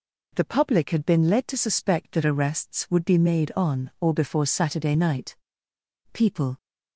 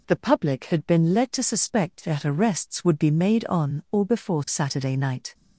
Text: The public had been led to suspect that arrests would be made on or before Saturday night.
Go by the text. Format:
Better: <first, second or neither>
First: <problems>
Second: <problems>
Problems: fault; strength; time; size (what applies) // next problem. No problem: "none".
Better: second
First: goes on to say "People"; slight; from 6.1 s on; 0.44 s long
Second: none